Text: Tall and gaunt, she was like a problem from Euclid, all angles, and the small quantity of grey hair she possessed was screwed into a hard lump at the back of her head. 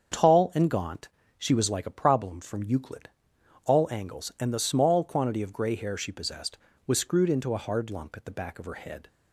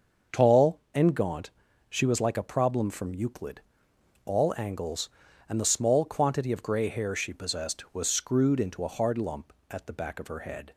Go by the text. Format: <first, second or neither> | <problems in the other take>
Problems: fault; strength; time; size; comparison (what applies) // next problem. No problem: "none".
neither | starts louder than the rest; the same in both